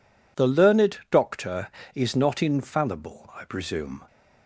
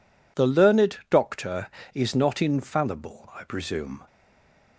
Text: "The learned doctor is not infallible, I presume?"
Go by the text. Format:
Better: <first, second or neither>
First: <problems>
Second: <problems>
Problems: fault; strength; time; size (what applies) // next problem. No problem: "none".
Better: first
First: none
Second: stays silent after the last word; slight; from 4.0 s on; 0.7 s long